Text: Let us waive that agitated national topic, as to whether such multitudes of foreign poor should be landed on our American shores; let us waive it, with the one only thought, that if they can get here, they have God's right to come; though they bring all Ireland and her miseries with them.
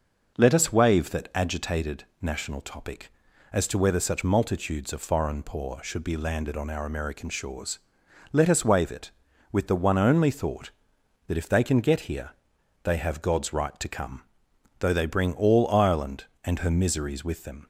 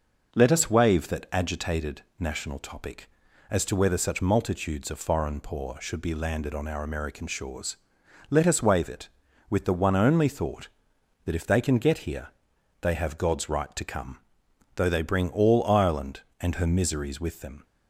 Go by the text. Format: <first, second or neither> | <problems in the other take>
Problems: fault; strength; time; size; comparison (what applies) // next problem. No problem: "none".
neither | none